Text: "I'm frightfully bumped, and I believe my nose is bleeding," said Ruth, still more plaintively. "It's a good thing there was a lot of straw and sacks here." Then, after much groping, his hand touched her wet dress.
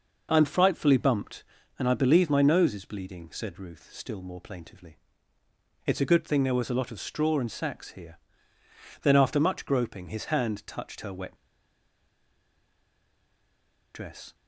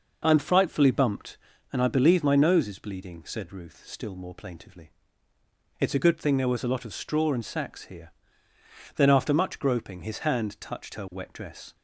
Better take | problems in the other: second | pauses between "wet" and "dress"; strong; at 11.3 s; 2.5 s long

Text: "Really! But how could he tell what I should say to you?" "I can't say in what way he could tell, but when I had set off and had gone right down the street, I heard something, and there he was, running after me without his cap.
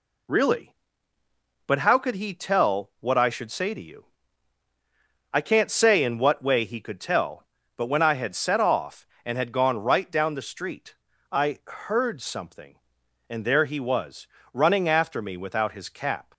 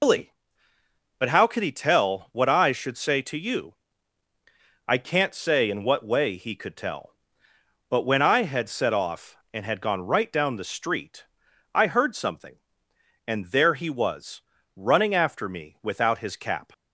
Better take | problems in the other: first | loses the start of "Really"; at 0.0 s; 160 ms

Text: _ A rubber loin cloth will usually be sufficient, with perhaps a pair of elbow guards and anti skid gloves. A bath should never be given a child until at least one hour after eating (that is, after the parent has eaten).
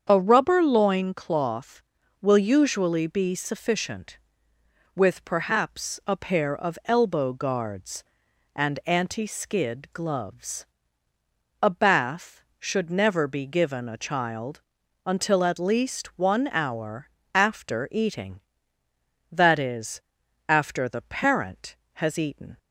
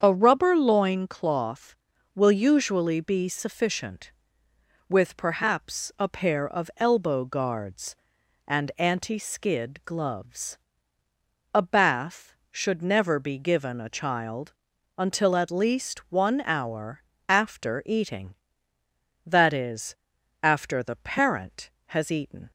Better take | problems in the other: neither | starts louder than the rest; strong; the same in both // pauses between "child" and "until"; the same in both // pauses between "hour" and "after"; slight; the same in both

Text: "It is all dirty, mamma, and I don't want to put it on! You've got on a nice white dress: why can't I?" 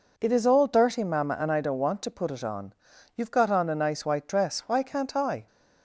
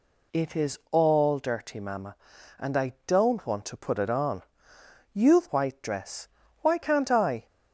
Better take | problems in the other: first | skips "got on a nice"; at 5.4 s

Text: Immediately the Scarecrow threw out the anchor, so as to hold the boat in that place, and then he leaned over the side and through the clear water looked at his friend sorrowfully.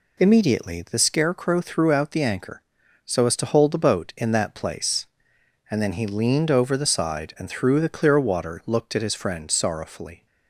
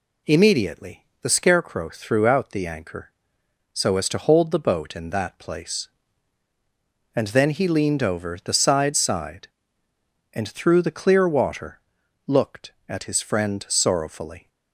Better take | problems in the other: first | pauses between "Immediately" and "the"; slight; at 1.0 s; 0.16 s long // says "side" twice; at 8.9 s // pauses between "water" and "looked"; noticeable; at 11.7 s; 0.48 s long

